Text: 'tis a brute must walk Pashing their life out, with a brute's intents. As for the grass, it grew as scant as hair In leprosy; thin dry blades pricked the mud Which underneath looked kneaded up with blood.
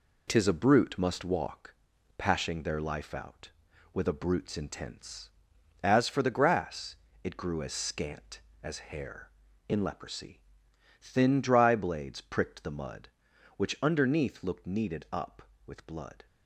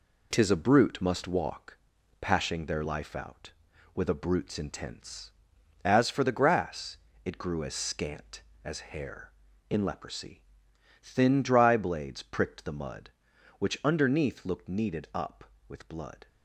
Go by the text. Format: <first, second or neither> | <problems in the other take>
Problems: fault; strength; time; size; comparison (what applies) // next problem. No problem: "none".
neither | pauses between "walk" and "Pashing"; noticeable; the same in both